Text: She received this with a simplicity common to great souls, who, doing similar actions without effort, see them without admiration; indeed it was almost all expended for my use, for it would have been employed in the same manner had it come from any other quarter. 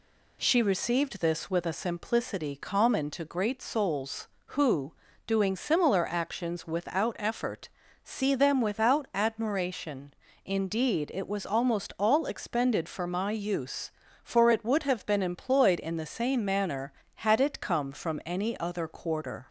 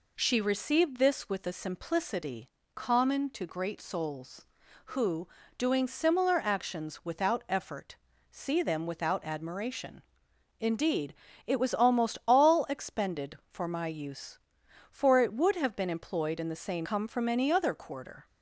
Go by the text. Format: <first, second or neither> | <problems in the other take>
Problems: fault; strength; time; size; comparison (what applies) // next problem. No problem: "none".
first | pauses between "simplicity" and "common"; slight; at 2.4 s; 0.26 s long // pauses between "indeed" and "it"; slight; at 11.1 s; 0.34 s long // skips "manner had it"; at 16.8 s